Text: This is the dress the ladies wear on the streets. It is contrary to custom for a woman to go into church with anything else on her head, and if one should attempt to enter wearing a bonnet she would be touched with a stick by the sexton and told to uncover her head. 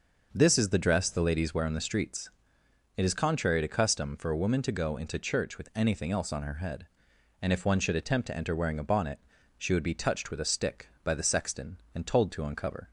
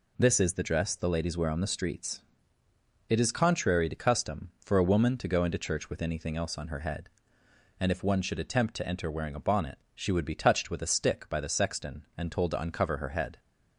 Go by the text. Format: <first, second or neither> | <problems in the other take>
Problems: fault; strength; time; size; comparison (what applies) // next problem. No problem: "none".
second | starts louder than the rest; until 1.3 s; 6 dB // pauses between "bonnet" and "she"; slight; at 9.2 s; 0.36 s long; slight in the second // stops before "her head"; at 12.8 s